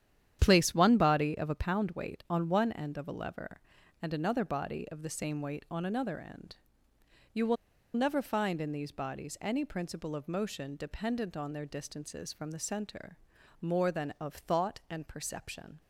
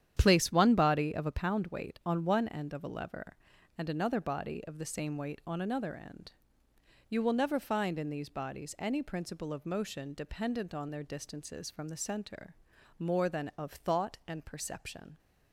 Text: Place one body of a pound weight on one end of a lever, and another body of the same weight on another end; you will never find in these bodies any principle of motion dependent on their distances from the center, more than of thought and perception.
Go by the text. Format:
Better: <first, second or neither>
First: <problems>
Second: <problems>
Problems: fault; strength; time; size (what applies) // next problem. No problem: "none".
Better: second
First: starts louder than the rest; strong; until 1.4 s; 10 dB // pauses between "will" and "never"; at 7.5 s; 0.40 s long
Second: starts louder than the rest; strong; until 1.1 s; 10 dB